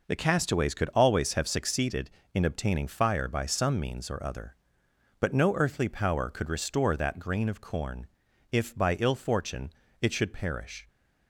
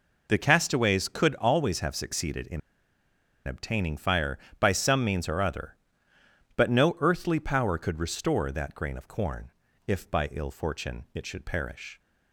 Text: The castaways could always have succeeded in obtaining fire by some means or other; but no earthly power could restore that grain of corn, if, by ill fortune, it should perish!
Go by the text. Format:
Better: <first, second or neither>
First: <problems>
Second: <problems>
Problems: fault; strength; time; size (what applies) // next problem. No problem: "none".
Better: first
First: none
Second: pauses between "in" and "obtaining"; noticeable; at 2.6 s; 0.86 s long